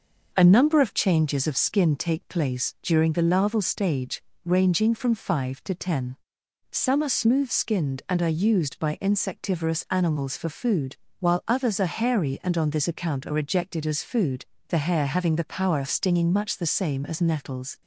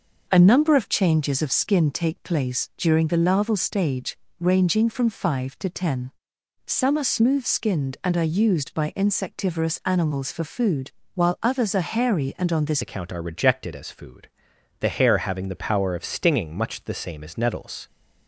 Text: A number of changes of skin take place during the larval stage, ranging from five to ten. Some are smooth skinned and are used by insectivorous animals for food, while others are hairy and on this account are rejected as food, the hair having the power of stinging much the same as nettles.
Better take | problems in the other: first | changes voice at "account"; from 12.8 s on; 5.0 s long

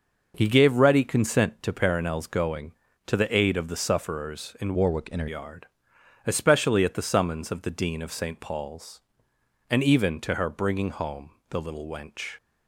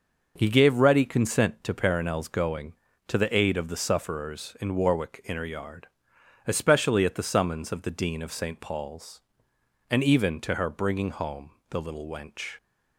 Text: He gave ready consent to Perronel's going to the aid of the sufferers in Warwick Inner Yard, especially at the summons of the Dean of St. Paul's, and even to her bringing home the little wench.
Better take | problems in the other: second | changes voice from "Warwick" to "Inner"; from 4.7 to 5.2 s; 0.5 s long // pauses between "home" and "the"; slight; at 11.3 s; 0.18 s long; slight in the second

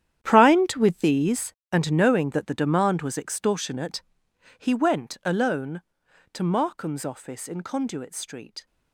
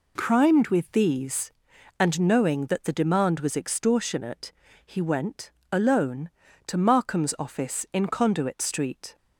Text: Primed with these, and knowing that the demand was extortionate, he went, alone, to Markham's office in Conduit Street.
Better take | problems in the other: second | gets quieter; strong; throughout; 15 dB

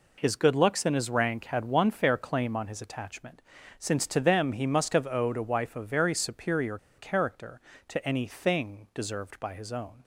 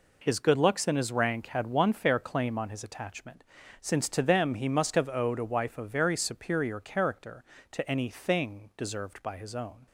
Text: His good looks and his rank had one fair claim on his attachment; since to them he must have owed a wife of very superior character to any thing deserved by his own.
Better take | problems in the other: second | pauses between "superior" and "character"; slight; at 6.7 s; 0.21 s long

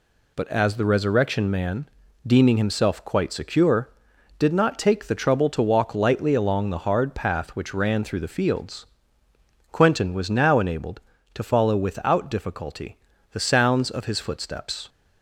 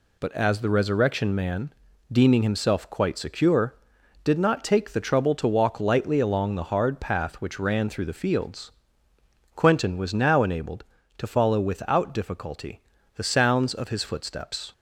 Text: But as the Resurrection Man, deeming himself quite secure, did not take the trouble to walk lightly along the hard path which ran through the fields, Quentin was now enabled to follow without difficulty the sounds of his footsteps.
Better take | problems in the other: neither | pauses between "difficulty" and "the"; slight; the same in both

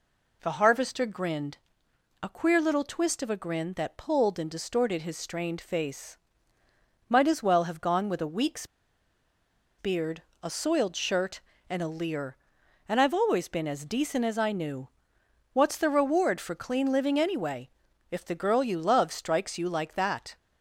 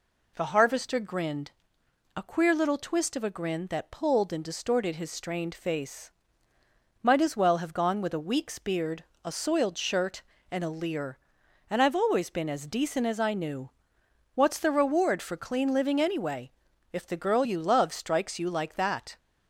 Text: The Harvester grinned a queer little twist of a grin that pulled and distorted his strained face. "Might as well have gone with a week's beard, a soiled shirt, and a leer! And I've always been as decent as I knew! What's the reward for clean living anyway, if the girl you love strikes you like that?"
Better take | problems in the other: second | pauses between "grinned" and "a"; noticeable; at 1.5 s; 0.64 s long; noticeable in the second // pauses between "week's" and "beard"; at 8.6 s; 1.1 s long

